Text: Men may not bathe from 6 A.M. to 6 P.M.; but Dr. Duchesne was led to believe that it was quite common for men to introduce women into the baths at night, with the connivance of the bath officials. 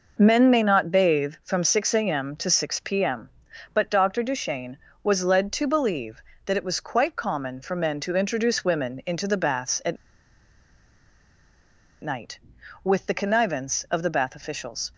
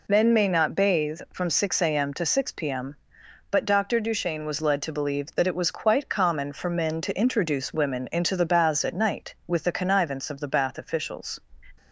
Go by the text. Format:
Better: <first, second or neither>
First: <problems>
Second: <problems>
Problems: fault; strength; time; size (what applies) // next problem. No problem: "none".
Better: second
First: pauses between "at" and "night"; strong; at 9.9 s; 2.0 s long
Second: none